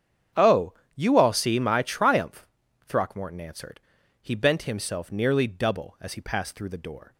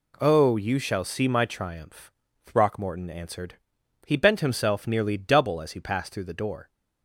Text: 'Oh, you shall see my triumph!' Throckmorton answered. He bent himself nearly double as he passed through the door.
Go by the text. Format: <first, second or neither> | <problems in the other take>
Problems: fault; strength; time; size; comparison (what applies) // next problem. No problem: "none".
second | starts louder than the rest; strong; until 1.5 s; 8 dB // says "all" for "shall"; at 1.1 s